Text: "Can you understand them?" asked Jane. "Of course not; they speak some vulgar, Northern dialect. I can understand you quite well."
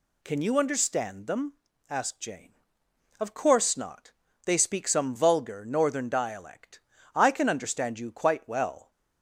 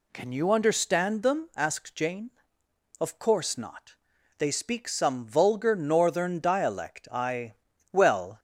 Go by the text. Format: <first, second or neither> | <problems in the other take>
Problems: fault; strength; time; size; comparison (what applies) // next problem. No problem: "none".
first | skips "can understand you quite"; at 7.7 s